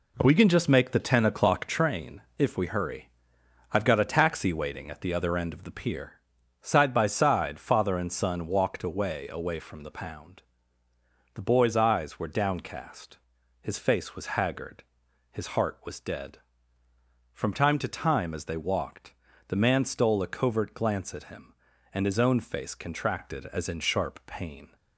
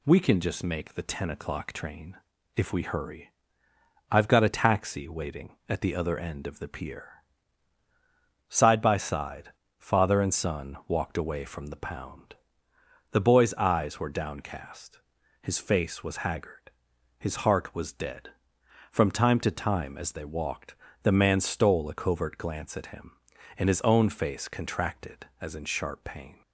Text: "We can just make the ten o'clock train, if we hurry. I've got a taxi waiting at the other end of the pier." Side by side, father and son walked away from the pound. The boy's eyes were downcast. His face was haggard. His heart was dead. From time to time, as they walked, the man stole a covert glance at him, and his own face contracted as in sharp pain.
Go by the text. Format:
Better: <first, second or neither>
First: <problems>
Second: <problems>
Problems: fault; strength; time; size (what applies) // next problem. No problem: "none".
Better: second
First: says "away" twice; at 9.2 s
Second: none